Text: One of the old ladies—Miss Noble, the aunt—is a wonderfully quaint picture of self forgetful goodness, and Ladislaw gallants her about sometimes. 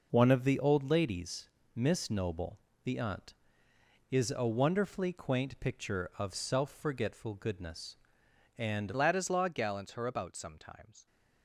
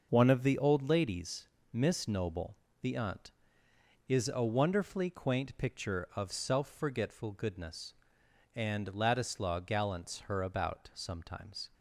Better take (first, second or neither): second